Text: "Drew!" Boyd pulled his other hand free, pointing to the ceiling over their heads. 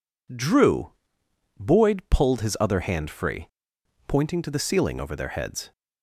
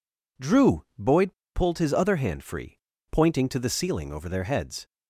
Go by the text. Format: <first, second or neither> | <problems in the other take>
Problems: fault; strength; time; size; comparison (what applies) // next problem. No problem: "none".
first | pauses between "Boyd" and "pulled"; slight; at 1.3 s; 0.23 s long